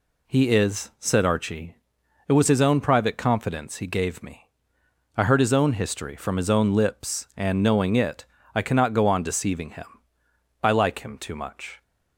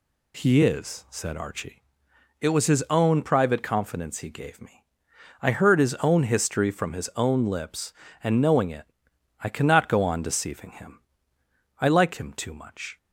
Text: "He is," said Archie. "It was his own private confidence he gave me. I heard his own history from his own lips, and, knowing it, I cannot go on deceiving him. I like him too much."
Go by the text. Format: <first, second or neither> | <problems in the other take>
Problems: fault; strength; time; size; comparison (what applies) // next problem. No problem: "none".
neither | none